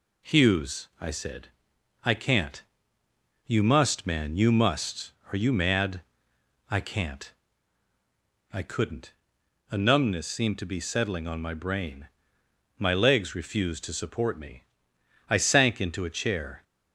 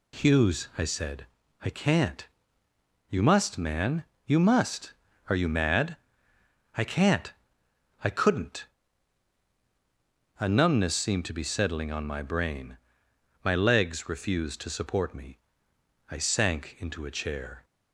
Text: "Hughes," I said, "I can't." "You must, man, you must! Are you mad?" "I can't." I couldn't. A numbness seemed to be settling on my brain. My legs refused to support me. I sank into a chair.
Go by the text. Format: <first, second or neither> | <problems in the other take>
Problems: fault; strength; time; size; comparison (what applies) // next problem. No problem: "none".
neither | none